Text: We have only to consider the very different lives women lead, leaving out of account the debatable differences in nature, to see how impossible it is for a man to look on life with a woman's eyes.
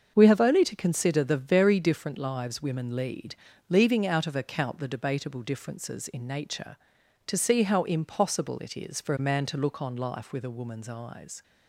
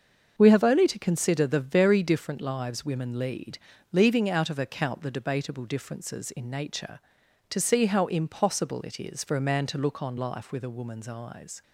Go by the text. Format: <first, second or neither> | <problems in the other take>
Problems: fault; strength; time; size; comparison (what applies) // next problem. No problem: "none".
neither | starts louder than the rest; the same in both